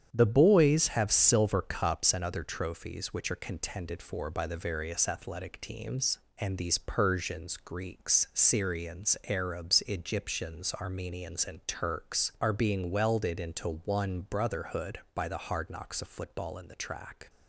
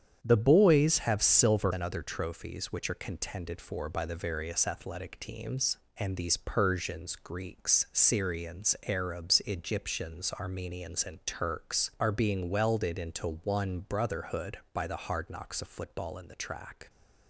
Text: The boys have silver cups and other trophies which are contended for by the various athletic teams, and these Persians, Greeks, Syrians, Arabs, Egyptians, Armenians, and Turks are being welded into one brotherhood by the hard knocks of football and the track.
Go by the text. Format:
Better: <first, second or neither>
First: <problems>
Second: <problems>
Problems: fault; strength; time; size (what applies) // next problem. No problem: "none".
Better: first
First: starts louder than the rest; strong; until 1.1 s; 8.5 dB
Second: starts louder than the rest; strong; until 1.2 s; 8 dB // skips "cups"; at 1.7 s